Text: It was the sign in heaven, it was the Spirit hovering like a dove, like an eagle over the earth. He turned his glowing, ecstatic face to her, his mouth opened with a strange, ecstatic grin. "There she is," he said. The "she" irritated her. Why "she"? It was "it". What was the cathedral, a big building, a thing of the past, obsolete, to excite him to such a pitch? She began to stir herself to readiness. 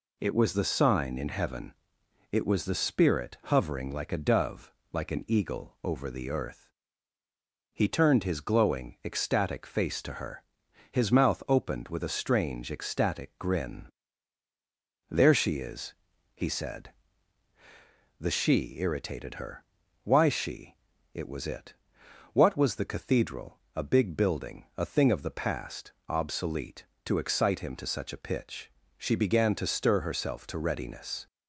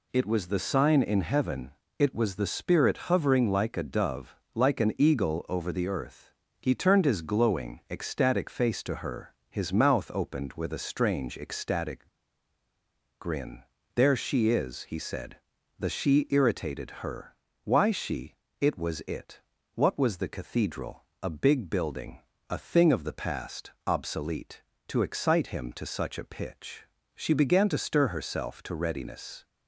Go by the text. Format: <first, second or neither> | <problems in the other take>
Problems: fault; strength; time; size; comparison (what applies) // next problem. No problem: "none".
first | pauses between "ecstatic" and "grin"; at 12.0 s; 1.1 s long